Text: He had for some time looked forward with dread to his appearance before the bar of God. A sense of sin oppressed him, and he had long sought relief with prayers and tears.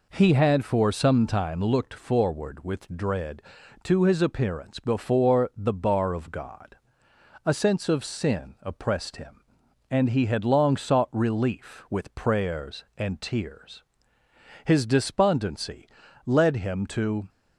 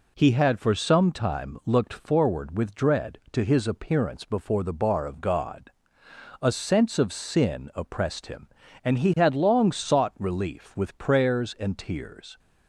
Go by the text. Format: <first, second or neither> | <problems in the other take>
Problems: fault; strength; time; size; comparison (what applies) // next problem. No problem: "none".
second | goes on to say "His despondency led him to"; strong; from 14.6 s on; 2.6 s long